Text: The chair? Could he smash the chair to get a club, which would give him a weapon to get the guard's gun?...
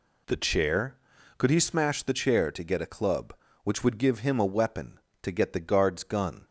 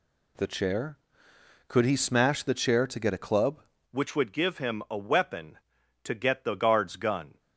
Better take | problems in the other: first | changes voice at "which"; from 3.9 s on; 3.4 s long

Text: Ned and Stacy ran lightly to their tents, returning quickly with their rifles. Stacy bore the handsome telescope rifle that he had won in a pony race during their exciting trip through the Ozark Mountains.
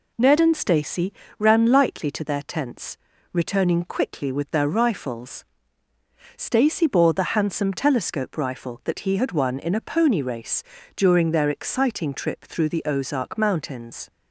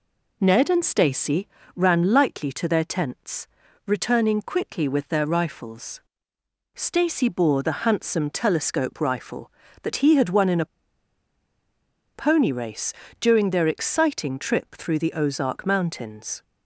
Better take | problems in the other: first | pauses between "Stacy" and "ran"; slight; at 1.4 s; 0.26 s long; slight in the first // pauses between "a" and "pony"; strong; at 10.6 s; 1.5 s long // pauses between "race" and "during"; slight; at 12.9 s; 0.28 s long; slight in the first

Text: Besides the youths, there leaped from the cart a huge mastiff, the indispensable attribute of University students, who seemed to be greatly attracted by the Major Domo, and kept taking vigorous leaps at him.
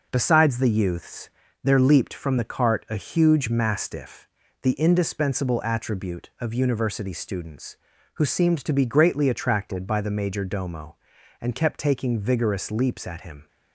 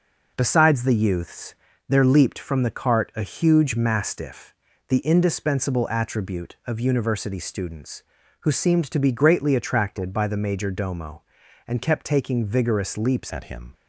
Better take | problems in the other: first | changes voice at "at"; from 13.3 s on; 0.4 s long

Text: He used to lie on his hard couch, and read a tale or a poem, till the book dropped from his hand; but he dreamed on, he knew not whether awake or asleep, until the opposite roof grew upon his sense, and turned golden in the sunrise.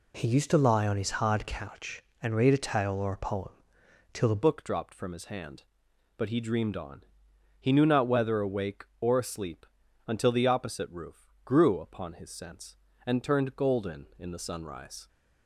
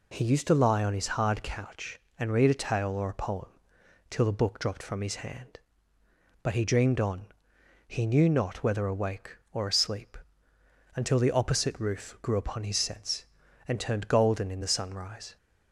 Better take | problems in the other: second | changes voice at "book"; from 4.4 s on; 10.6 s long

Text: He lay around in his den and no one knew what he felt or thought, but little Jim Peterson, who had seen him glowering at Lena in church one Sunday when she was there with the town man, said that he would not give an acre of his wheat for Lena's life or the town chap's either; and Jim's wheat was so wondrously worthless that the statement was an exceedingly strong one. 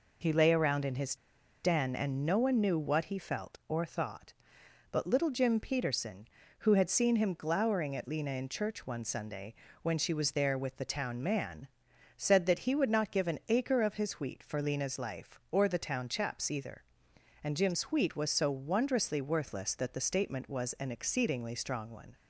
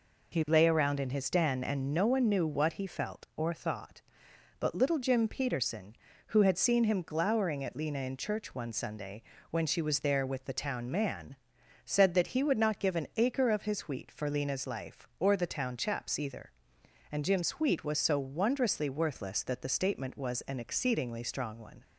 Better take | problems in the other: second | pauses between "his" and "den"; noticeable; at 1.1 s; 0.47 s long // pauses between "Sunday" and "when"; slight; at 9.5 s; 0.26 s long; slight in the second

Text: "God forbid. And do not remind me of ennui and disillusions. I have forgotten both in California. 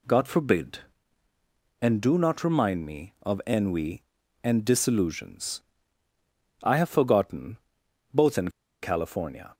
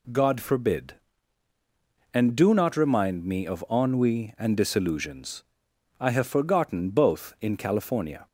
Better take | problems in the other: second | pauses between "forgotten" and "both"; noticeable; at 7.5 s; 0.54 s long // pauses between "in" and "California"; slight; at 8.4 s; 0.32 s long

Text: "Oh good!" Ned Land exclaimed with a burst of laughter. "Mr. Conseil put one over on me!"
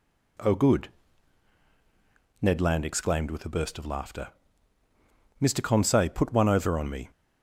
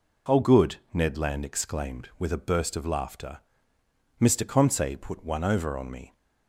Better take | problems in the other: neither | none

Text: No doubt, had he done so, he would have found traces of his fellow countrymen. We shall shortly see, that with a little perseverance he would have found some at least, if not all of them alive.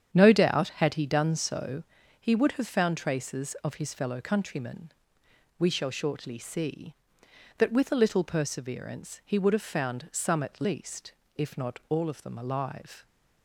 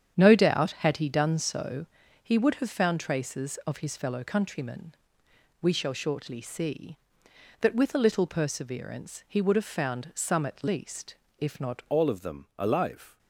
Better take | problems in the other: first | starts louder than the rest; strong; until 1.1 s; 8.5 dB; strong in the first // changes voice at "all"; from 11.9 s on; 1.2 s long

